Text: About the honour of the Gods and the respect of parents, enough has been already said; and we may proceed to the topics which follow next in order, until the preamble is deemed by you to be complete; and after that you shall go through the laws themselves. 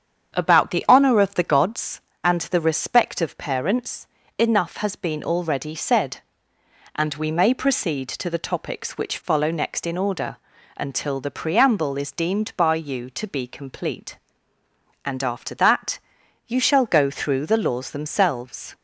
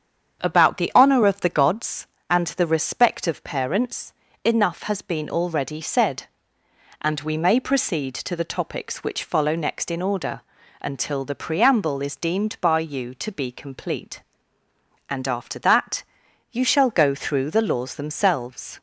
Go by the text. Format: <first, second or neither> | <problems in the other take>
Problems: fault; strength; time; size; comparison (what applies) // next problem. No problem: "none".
neither | starts louder than the rest; strong; the same in both // pauses between "that" and "you"; noticeable; the same in both